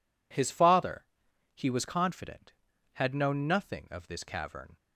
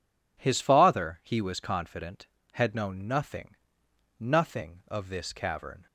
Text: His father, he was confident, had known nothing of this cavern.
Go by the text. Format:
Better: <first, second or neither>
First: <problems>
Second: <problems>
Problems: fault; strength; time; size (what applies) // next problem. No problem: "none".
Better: first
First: none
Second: says "nothing" twice; at 4.1 s